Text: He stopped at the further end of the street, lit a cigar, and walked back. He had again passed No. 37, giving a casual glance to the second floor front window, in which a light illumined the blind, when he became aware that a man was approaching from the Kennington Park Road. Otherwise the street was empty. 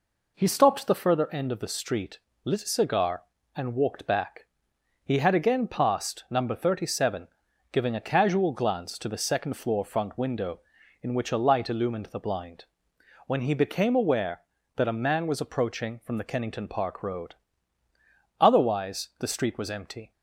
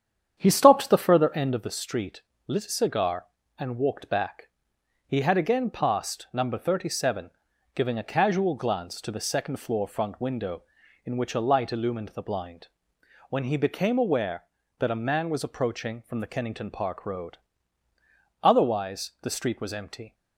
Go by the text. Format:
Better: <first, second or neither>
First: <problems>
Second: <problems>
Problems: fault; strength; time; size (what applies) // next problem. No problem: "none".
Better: first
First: none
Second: starts louder than the rest; strong; until 1.7 s; 8.5 dB